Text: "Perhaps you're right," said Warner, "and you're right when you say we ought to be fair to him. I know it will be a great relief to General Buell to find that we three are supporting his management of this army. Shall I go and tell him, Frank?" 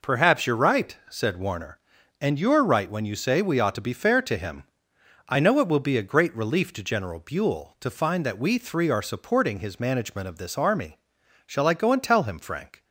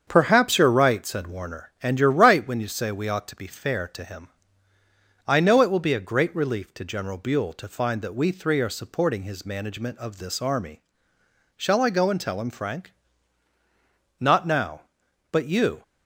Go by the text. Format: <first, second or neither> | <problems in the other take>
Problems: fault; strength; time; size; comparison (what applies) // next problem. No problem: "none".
first | starts louder than the rest; strong; until 1.0 s; 7.5 dB // goes on to say "Not now but you"; from 14.2 s on; 1.6 s long